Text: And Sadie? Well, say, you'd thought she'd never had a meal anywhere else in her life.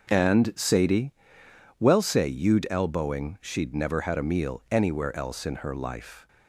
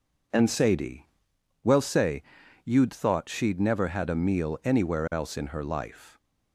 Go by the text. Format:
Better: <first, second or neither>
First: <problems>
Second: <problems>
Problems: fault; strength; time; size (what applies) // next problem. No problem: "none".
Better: second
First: says "elbowing" for "thought"; at 2.7 s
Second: none